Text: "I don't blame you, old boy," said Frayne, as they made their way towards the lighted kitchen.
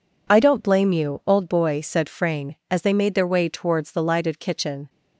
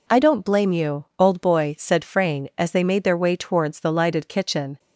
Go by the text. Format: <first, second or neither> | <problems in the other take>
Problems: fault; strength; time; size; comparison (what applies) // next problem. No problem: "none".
neither | none